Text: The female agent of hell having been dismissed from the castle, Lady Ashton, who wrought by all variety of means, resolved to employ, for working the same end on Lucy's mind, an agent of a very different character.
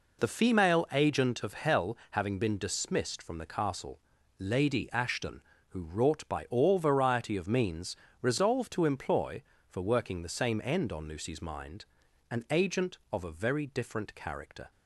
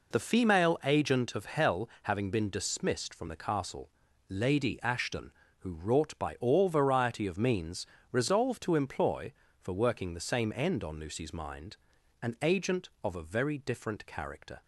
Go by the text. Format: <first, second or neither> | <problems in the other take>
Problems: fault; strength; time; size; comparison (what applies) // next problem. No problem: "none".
neither | none